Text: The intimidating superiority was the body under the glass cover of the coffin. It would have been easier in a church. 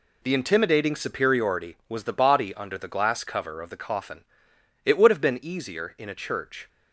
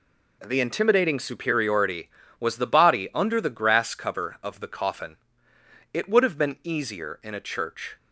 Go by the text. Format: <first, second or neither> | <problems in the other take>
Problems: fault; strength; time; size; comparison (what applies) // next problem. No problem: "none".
first | says "grass" for "glass"; at 3.4 s